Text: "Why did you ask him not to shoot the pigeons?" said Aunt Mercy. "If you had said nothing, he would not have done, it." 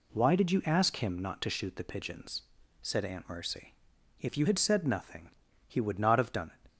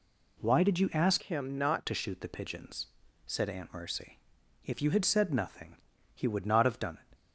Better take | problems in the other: first | changes voice from "him" to "not"; from 1.2 to 1.8 s; 0.6 s long

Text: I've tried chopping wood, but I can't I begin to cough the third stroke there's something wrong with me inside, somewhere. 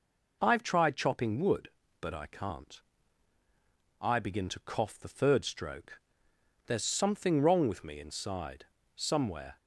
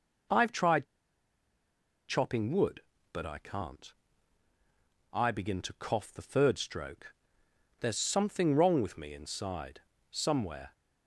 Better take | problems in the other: first | pauses between "tried" and "chopping"; at 0.8 s; 1.2 s long // pauses between "can't" and "I"; at 3.9 s; 1.2 s long; also in the first // pauses between "stroke" and "there's"; noticeable; at 7.1 s; 0.66 s long; noticeable in the first

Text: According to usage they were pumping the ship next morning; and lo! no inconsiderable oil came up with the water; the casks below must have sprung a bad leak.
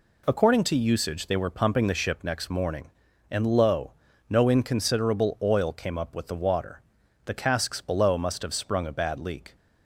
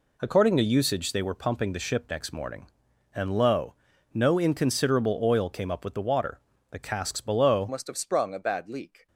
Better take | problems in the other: first | changes voice at "must"; from 7.6 s on; 1.4 s long

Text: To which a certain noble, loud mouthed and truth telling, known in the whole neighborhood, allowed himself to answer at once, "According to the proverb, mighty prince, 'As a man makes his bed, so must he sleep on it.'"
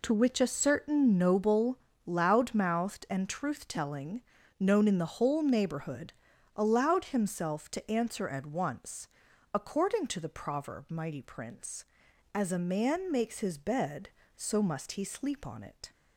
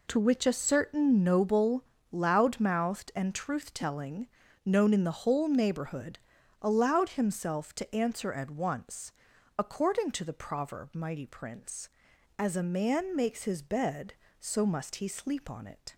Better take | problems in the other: neither | none

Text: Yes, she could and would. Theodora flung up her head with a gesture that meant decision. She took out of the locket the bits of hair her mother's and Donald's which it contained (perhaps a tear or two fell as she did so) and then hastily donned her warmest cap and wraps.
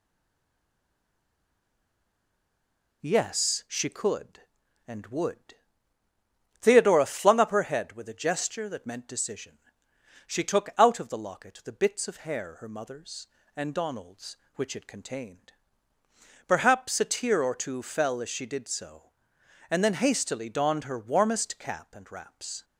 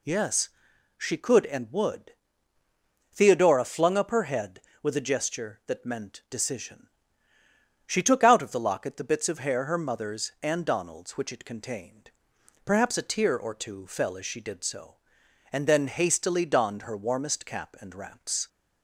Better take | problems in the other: second | stays silent before the first word; strong; until 3.0 s; 3.0 s long

